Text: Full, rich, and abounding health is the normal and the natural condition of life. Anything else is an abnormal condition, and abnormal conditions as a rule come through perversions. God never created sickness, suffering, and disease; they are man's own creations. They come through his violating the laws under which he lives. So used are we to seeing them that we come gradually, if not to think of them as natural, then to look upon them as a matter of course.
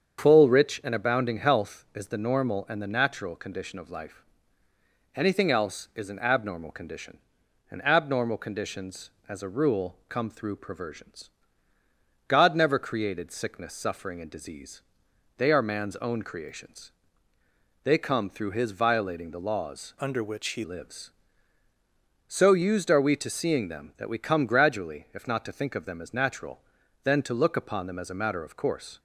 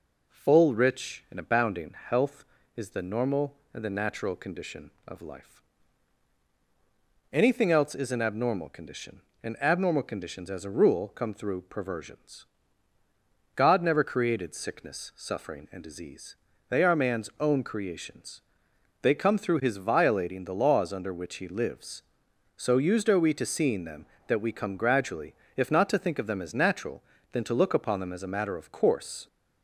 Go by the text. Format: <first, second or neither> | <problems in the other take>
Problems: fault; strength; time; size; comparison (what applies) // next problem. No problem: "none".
second | starts louder than the rest; strong; until 1.2 s; 7.5 dB // changes voice from "under" to "he"; from 20.0 to 20.6 s; 0.6 s long